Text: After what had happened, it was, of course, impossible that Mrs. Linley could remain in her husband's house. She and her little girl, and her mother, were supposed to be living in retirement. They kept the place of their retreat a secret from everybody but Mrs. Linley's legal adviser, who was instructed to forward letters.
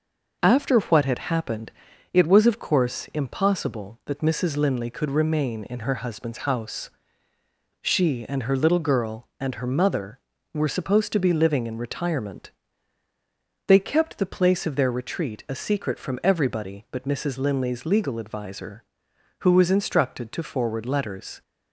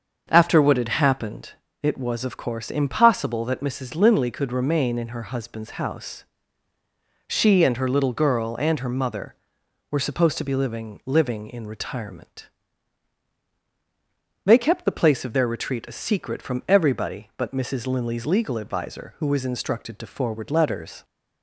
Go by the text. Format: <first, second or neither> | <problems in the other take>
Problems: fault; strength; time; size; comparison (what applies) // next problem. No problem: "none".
first | starts louder than the rest; until 1.3 s; 6.5 dB // says "living" twice; at 11.0 s